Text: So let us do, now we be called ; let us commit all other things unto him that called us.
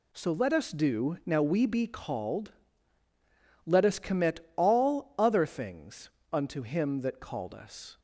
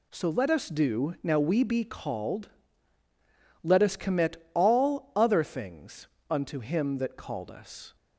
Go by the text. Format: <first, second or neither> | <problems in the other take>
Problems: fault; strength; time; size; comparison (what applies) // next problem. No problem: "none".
neither | pauses between "commit" and "all"; slight; the same in both // pauses between "things" and "unto"; slight; the same in both